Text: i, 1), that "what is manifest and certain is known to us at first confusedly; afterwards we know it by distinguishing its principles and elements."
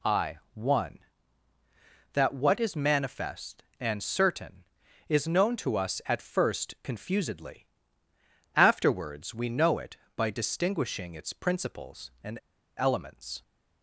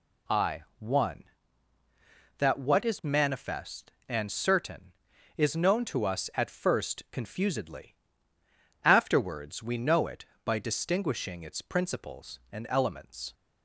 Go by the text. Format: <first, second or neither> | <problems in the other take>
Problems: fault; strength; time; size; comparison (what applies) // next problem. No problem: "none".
second | pauses between "and" and "elements"; at 12.3 s; 0.39 s long